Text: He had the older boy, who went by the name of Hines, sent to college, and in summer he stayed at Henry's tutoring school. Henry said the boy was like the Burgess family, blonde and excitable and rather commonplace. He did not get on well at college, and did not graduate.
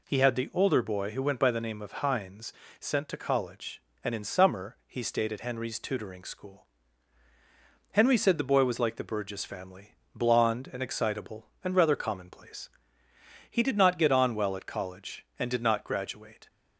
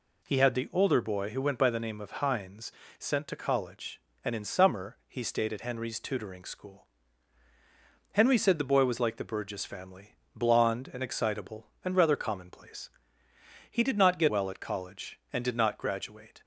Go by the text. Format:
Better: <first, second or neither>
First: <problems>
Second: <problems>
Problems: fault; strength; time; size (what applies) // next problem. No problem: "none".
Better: first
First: none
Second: skips "on"; at 14.2 s